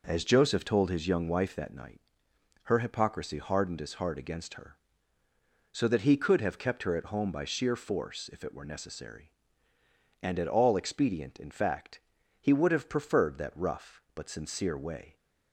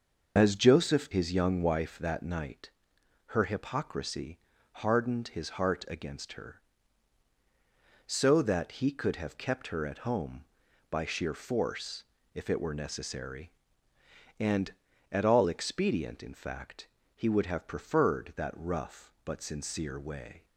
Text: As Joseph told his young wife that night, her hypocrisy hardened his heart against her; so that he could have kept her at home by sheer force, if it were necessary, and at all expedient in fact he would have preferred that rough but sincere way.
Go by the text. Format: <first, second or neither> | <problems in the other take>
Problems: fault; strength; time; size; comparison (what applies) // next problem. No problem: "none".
first | starts louder than the rest; noticeable; until 1.3 s; 6 dB // skips "told"; at 1.0 s // pauses between "hypocrisy" and "hardened"; slight; at 4.3 s; 0.32 s long // pauses between "fact" and "he"; slight; at 16.8 s; 0.30 s long; also in the first